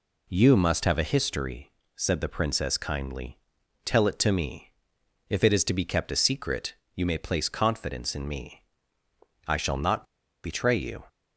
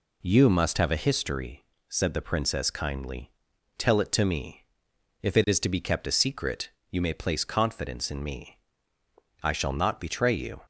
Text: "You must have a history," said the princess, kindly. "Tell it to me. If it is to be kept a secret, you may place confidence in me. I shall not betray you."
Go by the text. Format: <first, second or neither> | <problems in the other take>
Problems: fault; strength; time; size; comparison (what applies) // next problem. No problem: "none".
second | pauses between "not" and "betray"; at 10.0 s; 0.40 s long